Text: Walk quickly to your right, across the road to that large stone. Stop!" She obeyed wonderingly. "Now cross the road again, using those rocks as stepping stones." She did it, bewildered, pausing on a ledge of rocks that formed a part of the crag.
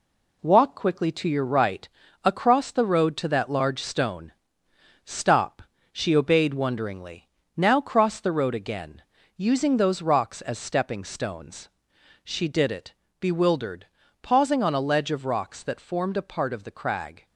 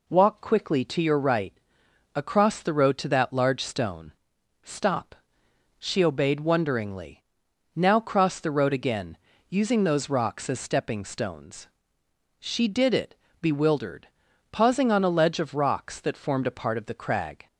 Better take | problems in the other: second | gets quieter; noticeable; throughout; 5 dB

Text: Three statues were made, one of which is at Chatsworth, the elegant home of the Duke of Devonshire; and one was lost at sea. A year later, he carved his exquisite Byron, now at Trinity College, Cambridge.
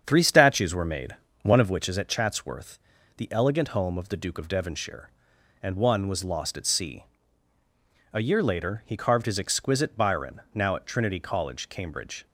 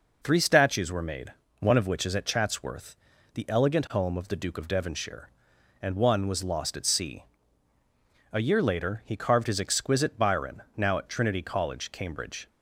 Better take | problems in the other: second | starts louder than the rest; strong; until 1.9 s; 7.5 dB

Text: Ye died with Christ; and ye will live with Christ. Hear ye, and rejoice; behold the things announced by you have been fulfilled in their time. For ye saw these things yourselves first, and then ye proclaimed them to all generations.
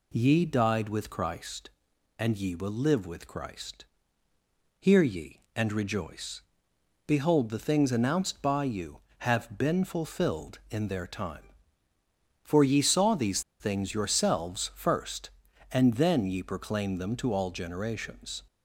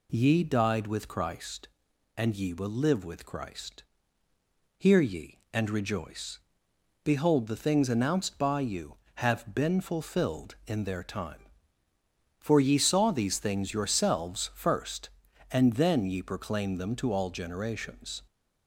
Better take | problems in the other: second | pauses between "these" and "things"; slight; at 13.4 s; 0.19 s long

